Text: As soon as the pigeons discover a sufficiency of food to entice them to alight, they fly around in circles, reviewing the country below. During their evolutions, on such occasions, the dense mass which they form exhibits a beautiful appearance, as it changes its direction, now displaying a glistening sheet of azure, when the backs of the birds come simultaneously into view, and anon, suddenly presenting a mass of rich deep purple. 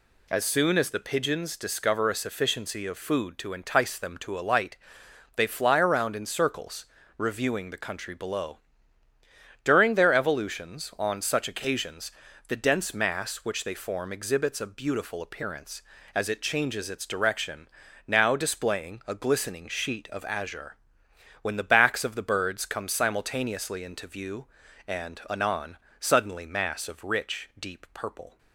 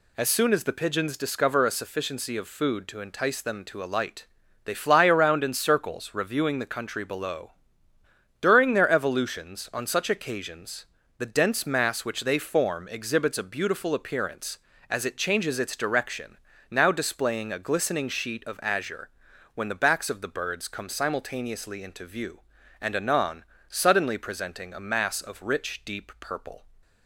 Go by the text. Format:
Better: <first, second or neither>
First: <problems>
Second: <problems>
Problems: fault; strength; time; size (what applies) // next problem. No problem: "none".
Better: second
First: skips "presenting a"; at 26.4 s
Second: none